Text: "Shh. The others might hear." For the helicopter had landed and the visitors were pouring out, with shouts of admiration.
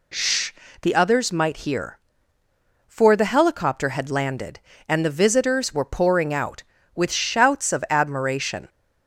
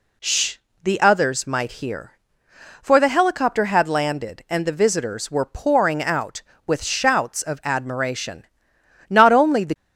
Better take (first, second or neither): first